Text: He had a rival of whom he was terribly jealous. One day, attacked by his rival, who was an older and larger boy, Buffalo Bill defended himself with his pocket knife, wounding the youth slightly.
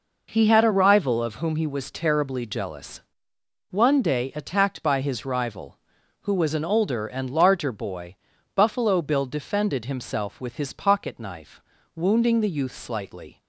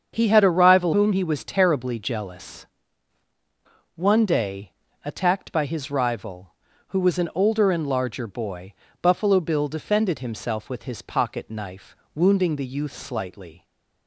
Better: first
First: none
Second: starts louder than the rest; until 1.1 s; 7 dB // skips "of"; at 0.9 s

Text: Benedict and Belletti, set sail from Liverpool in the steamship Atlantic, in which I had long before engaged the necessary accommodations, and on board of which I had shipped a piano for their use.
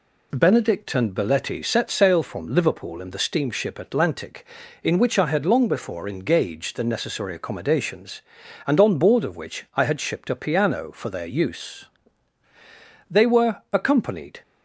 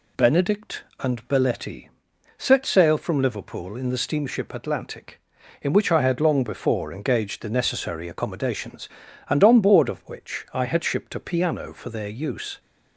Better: second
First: goes on to say "They were accompanied"; from 13.0 s on; 1.3 s long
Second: none

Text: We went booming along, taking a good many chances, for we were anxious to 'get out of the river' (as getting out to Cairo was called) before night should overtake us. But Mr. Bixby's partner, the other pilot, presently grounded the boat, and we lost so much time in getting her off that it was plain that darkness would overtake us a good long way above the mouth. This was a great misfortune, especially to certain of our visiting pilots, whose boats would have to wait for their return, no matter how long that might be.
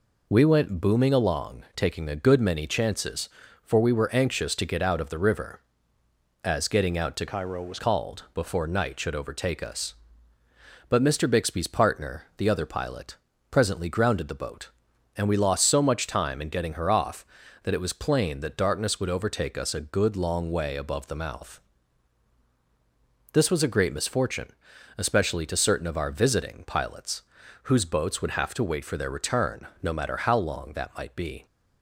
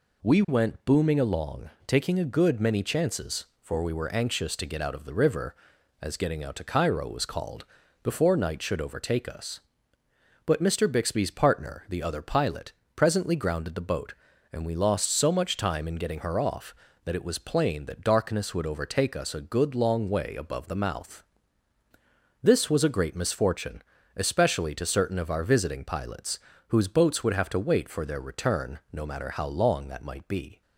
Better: second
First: changes voice from "Cairo" to "was"; from 7.2 to 7.7 s; 0.5 s long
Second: none

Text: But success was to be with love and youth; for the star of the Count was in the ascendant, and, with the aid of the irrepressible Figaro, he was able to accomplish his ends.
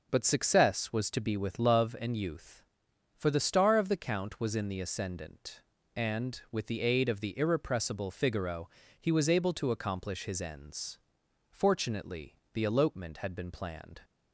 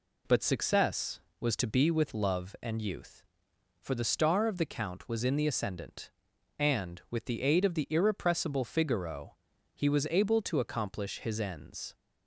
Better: second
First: goes on to say "Fortunately the elopement had been planned"; strong; from 11.4 s on; 2.5 s long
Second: none

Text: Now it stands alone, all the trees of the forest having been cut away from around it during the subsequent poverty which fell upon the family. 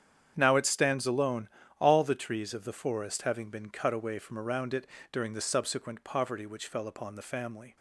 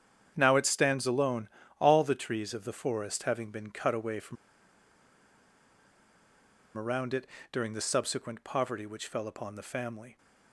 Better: first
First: starts louder than the rest; strong; until 1.3 s; 8.5 dB // pauses between "it" and "during"; slight; at 4.8 s; 0.24 s long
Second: starts louder than the rest; strong; until 1.3 s; 8.5 dB // pauses between "from" and "around"; strong; at 4.3 s; 2.4 s long // pauses between "it" and "during"; slight; at 7.2 s; 0.24 s long

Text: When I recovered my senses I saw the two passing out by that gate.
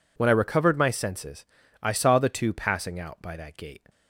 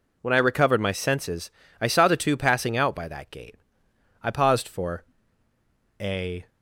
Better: first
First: pauses between "senses" and "I"; at 1.4 s; 0.38 s long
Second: pauses between "senses" and "I"; slight; at 1.4 s; 0.30 s long // goes on to say "I paused for a"; strong; from 4.2 s on; 2.2 s long

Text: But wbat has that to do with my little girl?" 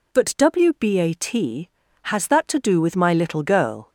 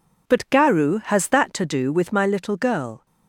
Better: first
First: none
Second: says "garu" for "wbat"; at 0.4 s

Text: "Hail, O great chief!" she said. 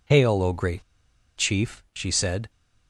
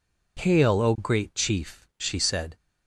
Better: second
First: pauses between "great" and "chief"; noticeable; at 0.8 s; 0.54 s long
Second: none

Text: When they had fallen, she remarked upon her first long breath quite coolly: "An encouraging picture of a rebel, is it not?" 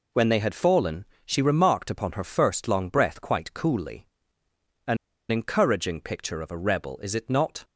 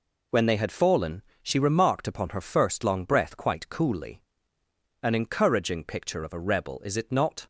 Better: second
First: pauses between "An" and "encouraging"; slight; at 4.9 s; 0.33 s long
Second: none

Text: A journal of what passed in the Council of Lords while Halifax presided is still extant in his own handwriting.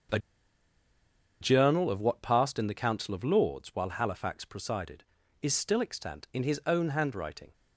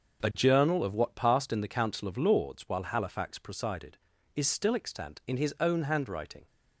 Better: second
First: starts louder than the rest; until 2.3 s; 7 dB // pauses between "A" and "journal"; at 0.1 s; 1.2 s long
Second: starts louder than the rest; until 1.2 s; 7 dB

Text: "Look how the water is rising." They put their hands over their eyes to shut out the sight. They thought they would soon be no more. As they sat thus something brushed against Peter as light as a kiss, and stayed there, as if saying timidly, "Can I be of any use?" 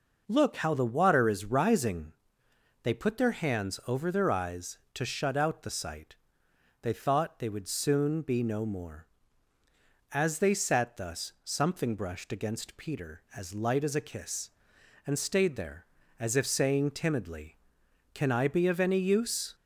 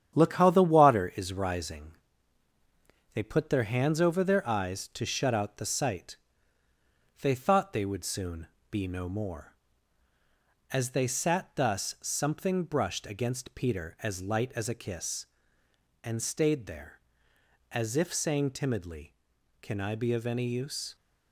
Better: first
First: none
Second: gets quieter; noticeable; throughout; 5.5 dB // pauses between "soon" and "be"; slight; at 8.4 s; 0.22 s long

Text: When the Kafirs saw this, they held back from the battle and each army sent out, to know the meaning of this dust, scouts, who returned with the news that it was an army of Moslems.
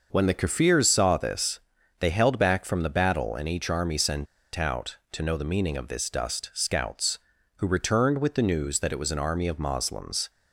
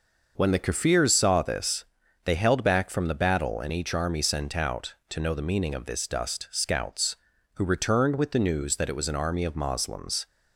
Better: second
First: pauses between "sent" and "out"; slight; at 4.2 s; 0.29 s long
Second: none

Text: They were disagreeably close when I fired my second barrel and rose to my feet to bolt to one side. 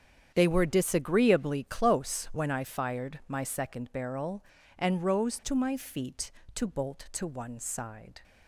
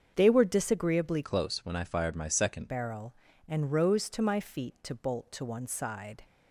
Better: first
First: starts louder than the rest; strong; until 1.3 s; 8.5 dB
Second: starts louder than the rest; strong; until 1.1 s; 7 dB // changes voice from "close" to "second"; from 1.2 to 2.6 s; 1.4 s long

